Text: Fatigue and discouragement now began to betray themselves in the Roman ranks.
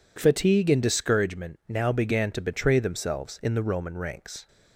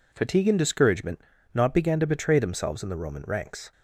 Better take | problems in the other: first | says "not" for "now"; at 1.5 s

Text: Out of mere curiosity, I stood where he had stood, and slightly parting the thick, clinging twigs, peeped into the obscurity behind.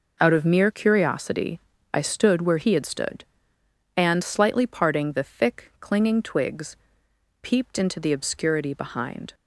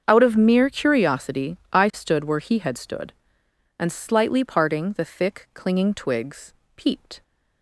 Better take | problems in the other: first | starts louder than the rest; strong; until 1.0 s; 7 dB // stops before "into the obscurity behind"; at 7.2 s

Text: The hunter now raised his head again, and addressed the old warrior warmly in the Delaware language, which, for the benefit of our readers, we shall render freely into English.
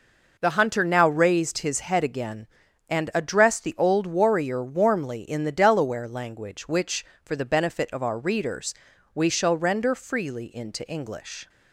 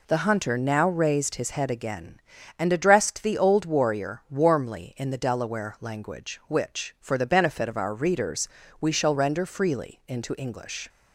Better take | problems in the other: neither | none

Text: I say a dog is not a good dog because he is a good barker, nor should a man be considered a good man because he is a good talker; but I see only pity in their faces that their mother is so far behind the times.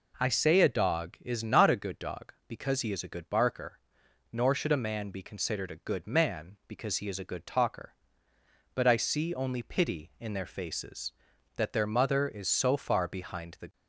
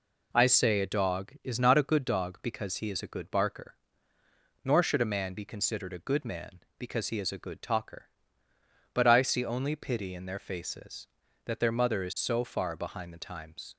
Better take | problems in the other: second | stops before "times"; at 13.7 s

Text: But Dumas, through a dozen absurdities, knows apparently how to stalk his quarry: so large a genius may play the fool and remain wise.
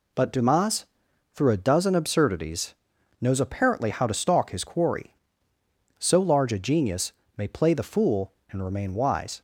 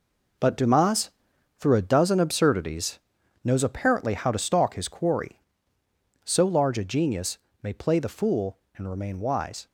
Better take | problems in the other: first | gets quieter; strong; throughout; 9 dB // pauses between "genius" and "may"; slight; at 7.3 s; 0.24 s long; slight in the first

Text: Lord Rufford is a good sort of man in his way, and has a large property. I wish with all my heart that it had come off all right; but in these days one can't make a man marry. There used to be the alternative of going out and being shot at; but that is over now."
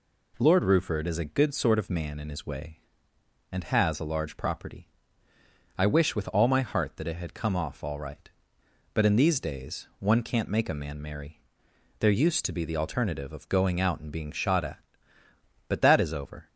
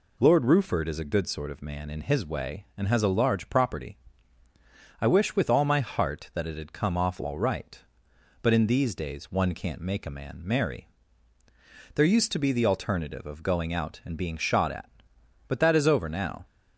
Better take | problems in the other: second | stops before "now"; at 16.4 s

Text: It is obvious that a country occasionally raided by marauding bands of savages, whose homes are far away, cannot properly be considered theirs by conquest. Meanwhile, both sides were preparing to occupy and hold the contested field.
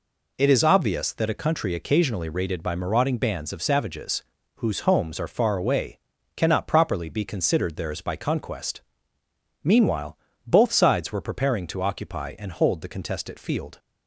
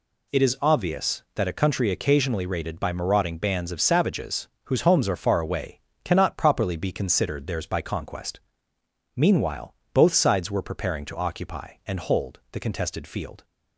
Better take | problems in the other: neither | none

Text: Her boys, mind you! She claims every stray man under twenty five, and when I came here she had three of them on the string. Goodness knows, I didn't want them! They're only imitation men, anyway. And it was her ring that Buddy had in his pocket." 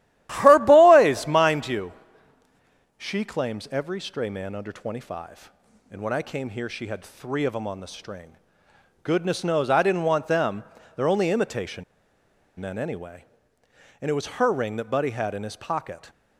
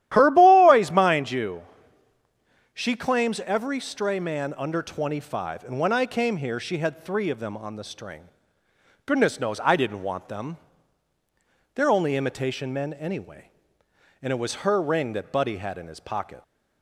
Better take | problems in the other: second | starts louder than the rest; strong; until 1.3 s; 13.5 dB; strong in the second // pauses between "imitation" and "men"; noticeable; at 11.8 s; 0.75 s long

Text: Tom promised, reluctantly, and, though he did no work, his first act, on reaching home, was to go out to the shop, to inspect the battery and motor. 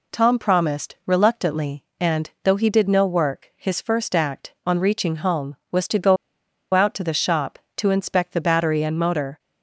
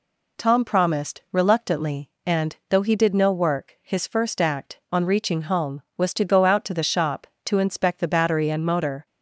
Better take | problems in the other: second | pauses between "go" and "out"; noticeable; at 6.1 s; 0.58 s long

